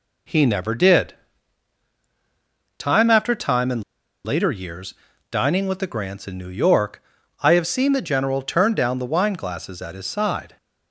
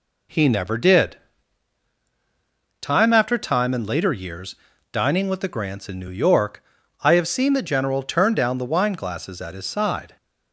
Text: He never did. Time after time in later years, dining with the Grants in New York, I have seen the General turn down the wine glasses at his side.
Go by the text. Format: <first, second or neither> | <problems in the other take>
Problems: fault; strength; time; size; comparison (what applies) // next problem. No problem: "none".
second | pauses between "in" and "later"; at 3.8 s; 0.43 s long